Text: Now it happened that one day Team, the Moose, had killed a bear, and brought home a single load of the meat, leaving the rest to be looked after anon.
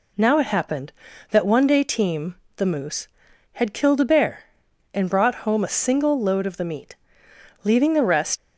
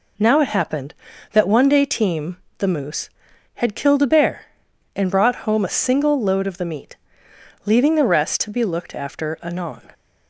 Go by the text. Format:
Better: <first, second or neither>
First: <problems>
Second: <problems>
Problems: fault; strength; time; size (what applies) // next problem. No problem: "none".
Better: second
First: stops before "to be looked after anon"; at 8.3 s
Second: none